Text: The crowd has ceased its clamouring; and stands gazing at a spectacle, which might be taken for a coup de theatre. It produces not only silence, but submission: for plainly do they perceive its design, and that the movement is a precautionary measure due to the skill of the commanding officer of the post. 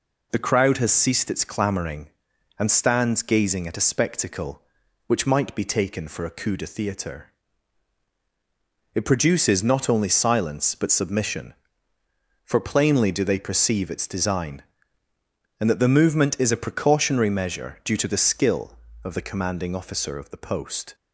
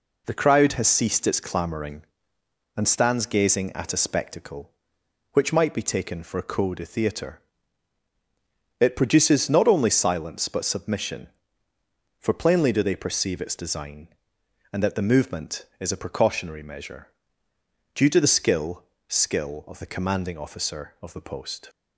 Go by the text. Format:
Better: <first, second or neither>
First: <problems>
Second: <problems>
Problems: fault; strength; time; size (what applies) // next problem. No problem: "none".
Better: first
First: none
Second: pauses between "measure" and "due"; noticeable; at 17.0 s; 0.84 s long // says "skill" twice; at 19.0 s